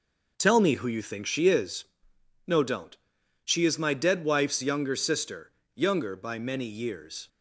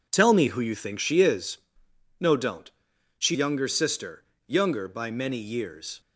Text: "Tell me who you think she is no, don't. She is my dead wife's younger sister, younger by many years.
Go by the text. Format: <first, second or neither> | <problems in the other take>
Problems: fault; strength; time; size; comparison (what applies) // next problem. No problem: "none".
first | pauses between "is" and "no"; noticeable; at 1.5 s; 0.60 s long; noticeable in the first // skips "is my dead wife's"; at 3.3 s